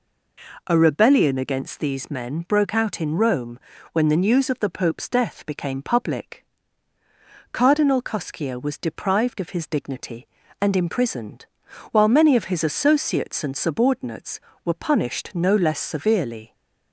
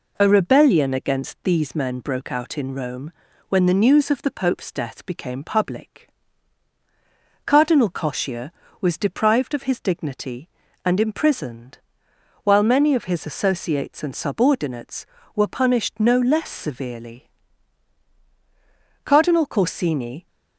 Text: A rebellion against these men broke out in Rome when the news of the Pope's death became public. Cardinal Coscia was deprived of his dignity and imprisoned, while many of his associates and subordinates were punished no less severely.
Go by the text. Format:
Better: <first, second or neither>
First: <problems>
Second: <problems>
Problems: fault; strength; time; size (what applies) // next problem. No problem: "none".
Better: first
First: pauses between "Rome" and "when"; slight; at 3.5 s; 0.34 s long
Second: pauses between "Rome" and "when"; at 3.1 s; 0.38 s long // goes on to say "Cardinal Corsini"; noticeable; from 19.0 s on; 1.2 s long